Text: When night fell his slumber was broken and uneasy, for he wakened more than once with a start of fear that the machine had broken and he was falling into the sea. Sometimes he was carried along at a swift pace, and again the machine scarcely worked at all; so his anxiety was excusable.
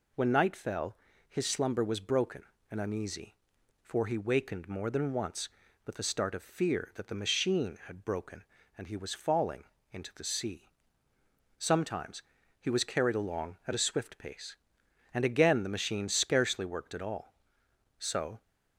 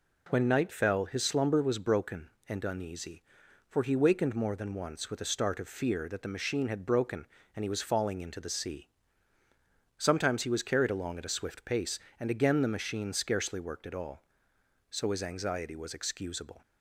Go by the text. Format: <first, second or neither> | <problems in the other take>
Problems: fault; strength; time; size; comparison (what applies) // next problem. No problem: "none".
second | pauses between "fell" and "his"; slight; at 0.9 s; 0.32 s long // pauses between "falling" and "into"; slight; at 9.6 s; 0.28 s long // pauses between "Sometimes" and "he"; at 12.2 s; 0.38 s long // stops before "his anxiety was excusable"; at 18.4 s